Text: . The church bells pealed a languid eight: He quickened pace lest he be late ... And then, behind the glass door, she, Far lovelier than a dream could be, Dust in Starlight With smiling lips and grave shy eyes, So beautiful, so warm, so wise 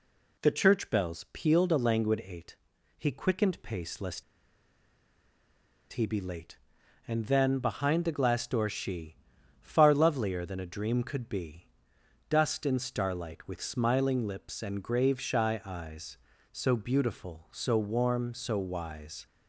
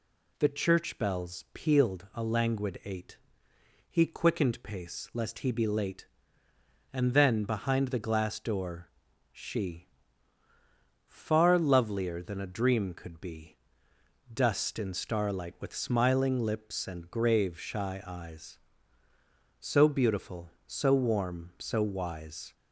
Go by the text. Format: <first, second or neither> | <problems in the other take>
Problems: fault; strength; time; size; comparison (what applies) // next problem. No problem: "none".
second | pauses between "lest" and "he"; strong; at 4.2 s; 1.6 s long